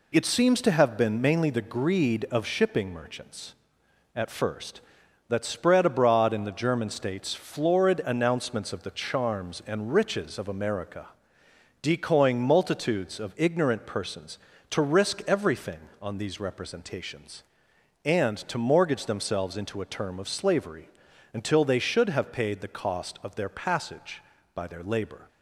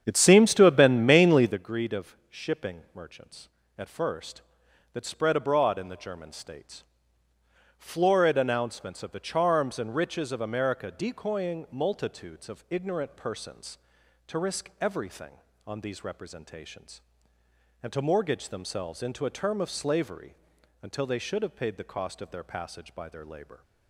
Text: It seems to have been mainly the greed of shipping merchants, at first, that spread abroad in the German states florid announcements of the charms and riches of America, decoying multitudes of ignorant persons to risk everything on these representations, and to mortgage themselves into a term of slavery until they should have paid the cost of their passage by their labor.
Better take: first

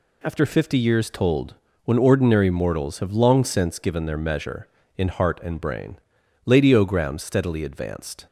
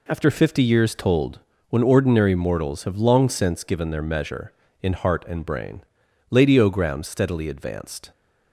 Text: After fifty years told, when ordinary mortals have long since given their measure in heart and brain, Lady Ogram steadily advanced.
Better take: first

